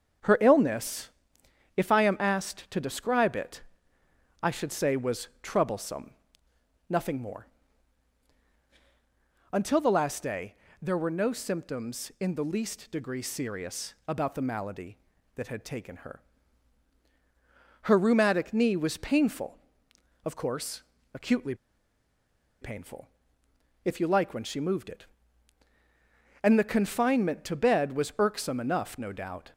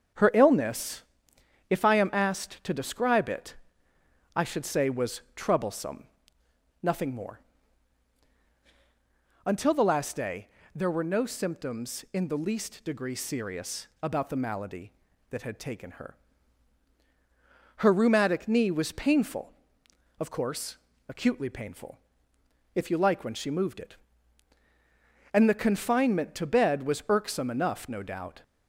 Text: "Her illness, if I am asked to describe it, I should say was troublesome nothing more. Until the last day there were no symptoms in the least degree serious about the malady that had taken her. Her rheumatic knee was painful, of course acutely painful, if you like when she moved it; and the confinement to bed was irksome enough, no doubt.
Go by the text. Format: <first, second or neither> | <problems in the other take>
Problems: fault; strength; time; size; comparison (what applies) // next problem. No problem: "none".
second | starts louder than the rest; until 1.9 s; 6.5 dB; also in the second // pauses between "troublesome" and "nothing"; noticeable; at 6.1 s; 0.78 s long; noticeable in the second // pauses between "day" and "there"; slight; at 10.5 s; 0.26 s long; slight in the second // pauses between "serious" and "about"; slight; at 13.9 s; 0.16 s long; slight in the second // pauses between "course" and "acutely"; slight; at 20.8 s; 0.32 s long; slight in the second // pauses between "acutely" and "painful"; at 21.5 s; 1.0 s long